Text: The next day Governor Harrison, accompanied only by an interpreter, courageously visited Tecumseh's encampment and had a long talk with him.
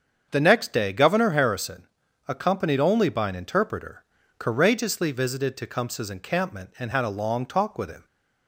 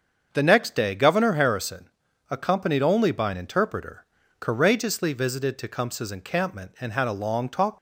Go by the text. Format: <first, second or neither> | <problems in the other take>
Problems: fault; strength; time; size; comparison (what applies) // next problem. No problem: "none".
first | starts louder than the rest; until 1.3 s; 7 dB; strong in the first // stops before "with him"; at 7.7 s